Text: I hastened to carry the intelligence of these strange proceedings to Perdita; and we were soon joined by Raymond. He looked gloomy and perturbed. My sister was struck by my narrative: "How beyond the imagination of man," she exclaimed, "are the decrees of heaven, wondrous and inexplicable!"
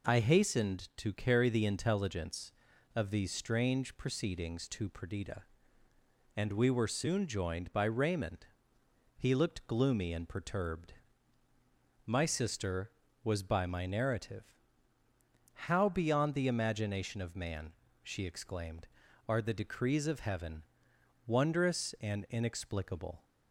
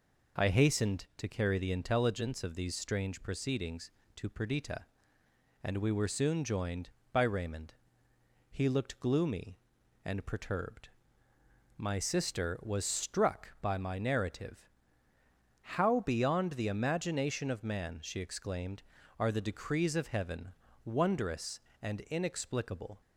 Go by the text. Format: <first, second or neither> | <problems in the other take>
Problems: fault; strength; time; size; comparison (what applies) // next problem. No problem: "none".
second | skips "struck"; at 13.4 s